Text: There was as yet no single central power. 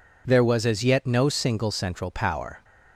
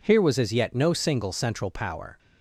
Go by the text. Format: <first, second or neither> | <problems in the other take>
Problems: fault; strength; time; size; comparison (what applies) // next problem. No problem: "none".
first | says "Here" for "There"; at 0.0 s